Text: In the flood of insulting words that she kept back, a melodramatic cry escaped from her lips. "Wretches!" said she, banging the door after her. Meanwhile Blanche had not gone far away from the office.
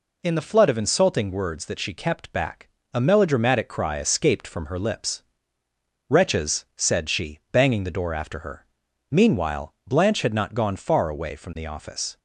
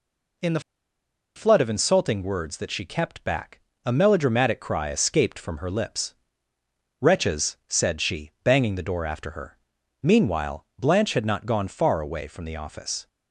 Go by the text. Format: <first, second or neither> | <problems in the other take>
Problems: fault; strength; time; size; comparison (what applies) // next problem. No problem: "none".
first | pauses between "the" and "flood"; noticeable; at 0.5 s; 0.75 s long